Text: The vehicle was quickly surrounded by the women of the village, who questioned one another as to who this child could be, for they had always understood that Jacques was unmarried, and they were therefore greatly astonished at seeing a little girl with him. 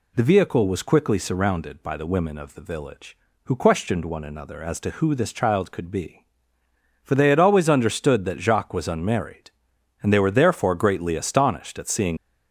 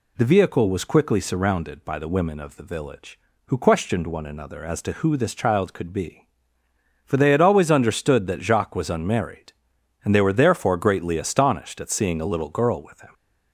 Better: second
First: stops before "a little girl with him"; at 12.1 s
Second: none

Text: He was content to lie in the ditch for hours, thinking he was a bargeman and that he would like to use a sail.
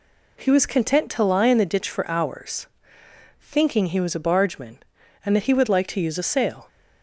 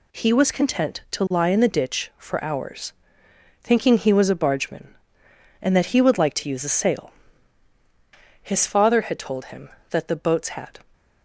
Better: first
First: none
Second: goes on to say "His father had told him that the boats had"; strong; from 8.4 s on; 2.3 s long

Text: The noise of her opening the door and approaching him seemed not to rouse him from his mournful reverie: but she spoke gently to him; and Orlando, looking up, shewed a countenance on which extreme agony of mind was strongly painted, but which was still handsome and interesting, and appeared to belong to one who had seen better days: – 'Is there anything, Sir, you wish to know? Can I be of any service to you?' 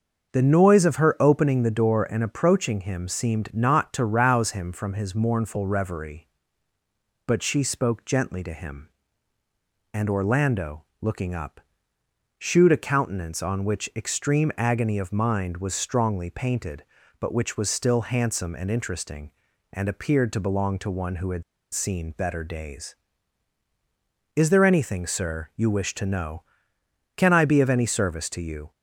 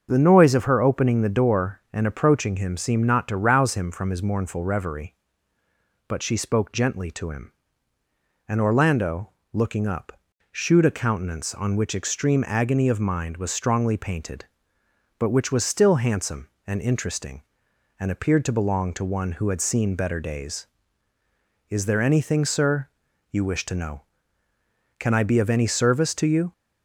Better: second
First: starts louder than the rest; until 1.3 s; 6.5 dB // pauses between "had" and "seen"; slight; at 21.4 s; 0.29 s long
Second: starts louder than the rest; until 1.1 s; 7 dB

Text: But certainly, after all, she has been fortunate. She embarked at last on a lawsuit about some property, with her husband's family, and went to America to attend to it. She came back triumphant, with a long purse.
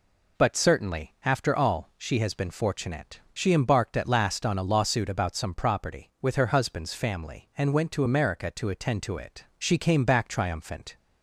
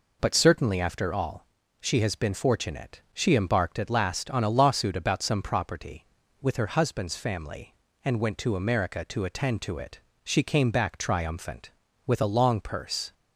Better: second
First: stops before "with a long purse"; at 10.9 s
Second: none

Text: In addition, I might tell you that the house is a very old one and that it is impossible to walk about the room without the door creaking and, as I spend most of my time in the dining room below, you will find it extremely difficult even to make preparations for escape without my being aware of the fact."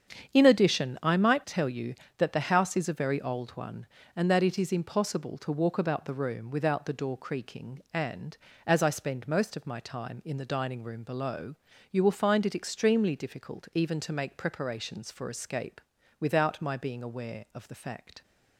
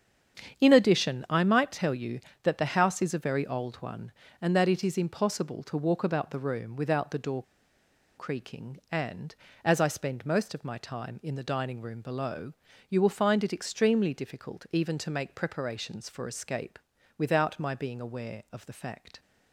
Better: first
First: starts louder than the rest; strong; until 1.3 s; 8 dB // pauses between "escape" and "without"; at 15.8 s; 0.38 s long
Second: starts louder than the rest; strong; until 1.6 s; 8 dB // pauses between "door" and "creaking"; noticeable; at 7.4 s; 0.75 s long // pauses between "escape" and "without"; at 16.7 s; 0.38 s long

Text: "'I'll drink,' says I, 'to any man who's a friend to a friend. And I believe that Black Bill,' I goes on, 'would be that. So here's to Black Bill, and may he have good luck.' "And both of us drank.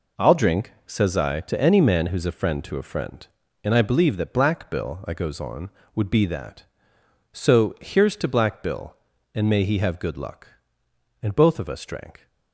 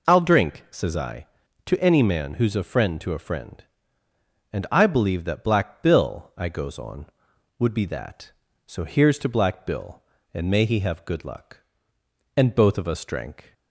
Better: neither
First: none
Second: none

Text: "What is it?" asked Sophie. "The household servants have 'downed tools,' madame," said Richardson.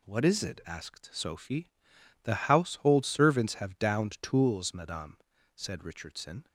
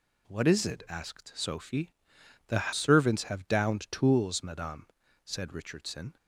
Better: first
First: none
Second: skips "household"; at 2.7 s

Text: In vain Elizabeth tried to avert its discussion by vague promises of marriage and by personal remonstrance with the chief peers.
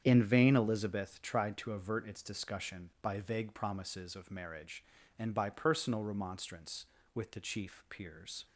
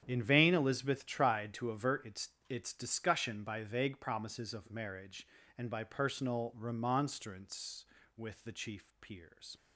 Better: first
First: starts louder than the rest; strong; until 1.0 s; 8.5 dB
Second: starts louder than the rest; strong; until 1.0 s; 9 dB // says "its" twice; at 2.4 s

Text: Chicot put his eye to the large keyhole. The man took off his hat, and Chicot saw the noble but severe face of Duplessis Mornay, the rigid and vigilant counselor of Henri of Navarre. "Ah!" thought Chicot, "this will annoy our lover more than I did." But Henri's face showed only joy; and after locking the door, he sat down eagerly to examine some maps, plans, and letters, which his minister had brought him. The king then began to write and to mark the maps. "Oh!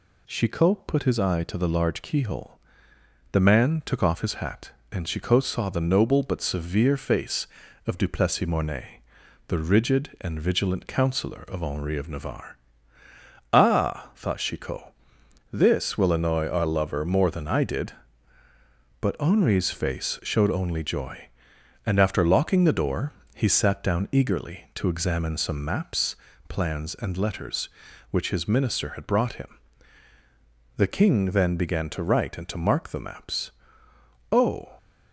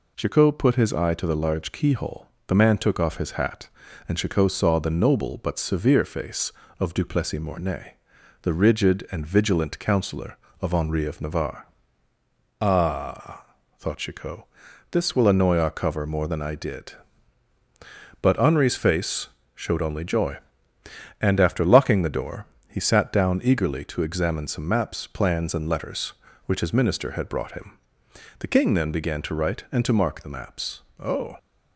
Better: first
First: none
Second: says "cover" for "lover"; at 15.7 s // pauses between "face" and "showed"; slight; at 19.2 s; 0.26 s long

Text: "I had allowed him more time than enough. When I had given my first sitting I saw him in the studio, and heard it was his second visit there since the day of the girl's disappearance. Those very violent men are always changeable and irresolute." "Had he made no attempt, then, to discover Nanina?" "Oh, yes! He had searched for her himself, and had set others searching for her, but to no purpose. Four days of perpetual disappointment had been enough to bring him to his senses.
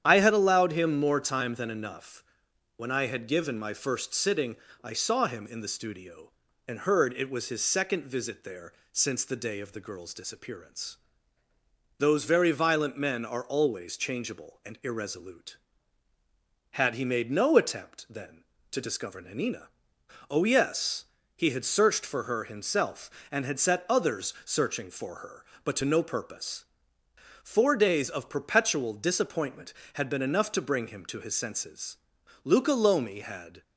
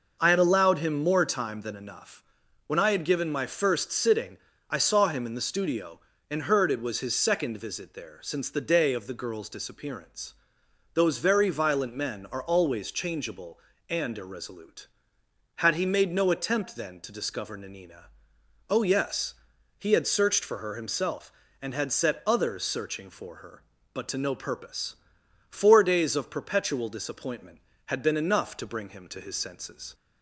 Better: second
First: starts louder than the rest; strong; until 1.0 s; 9.5 dB // pauses between "sitting" and "I"; slight; at 4.5 s; 0.26 s long // pauses between "there" and "since"; slight; at 8.7 s; 0.18 s long // goes on to say "Luca Lomi had"; noticeable; from 32.4 s on; 1.1 s long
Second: pauses between "sitting" and "I"; slight; at 4.3 s; 0.30 s long

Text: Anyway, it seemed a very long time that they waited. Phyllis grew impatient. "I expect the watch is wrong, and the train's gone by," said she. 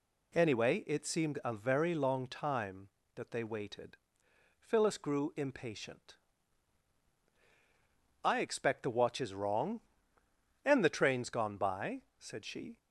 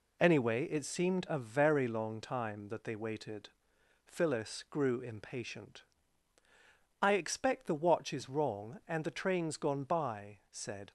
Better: first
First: none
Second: stops before "she"; at 10.8 s

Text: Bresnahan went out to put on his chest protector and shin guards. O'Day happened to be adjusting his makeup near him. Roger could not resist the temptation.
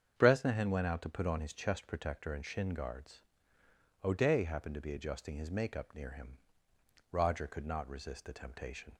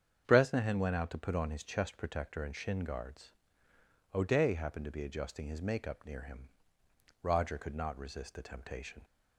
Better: neither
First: starts louder than the rest; strong; until 1.1 s; 7.5 dB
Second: starts louder than the rest; strong; until 1.2 s; 7.5 dB

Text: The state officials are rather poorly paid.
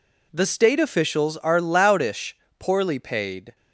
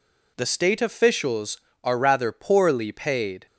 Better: second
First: says "loudish" for "rather"; at 1.5 s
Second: none

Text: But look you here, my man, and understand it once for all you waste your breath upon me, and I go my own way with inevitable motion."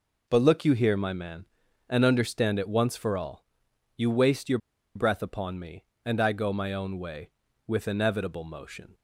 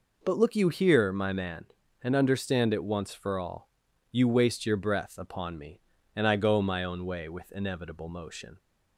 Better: second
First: pauses between "all" and "you"; noticeable; at 3.4 s; 0.54 s long // pauses between "your" and "breath"; at 4.5 s; 0.36 s long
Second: pauses between "all" and "you"; at 3.6 s; 0.44 s long

